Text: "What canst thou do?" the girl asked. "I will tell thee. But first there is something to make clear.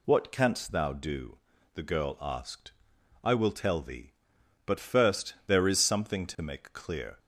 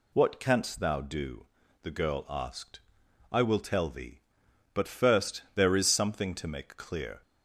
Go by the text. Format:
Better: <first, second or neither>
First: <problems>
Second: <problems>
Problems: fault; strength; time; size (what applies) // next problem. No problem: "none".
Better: neither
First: none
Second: none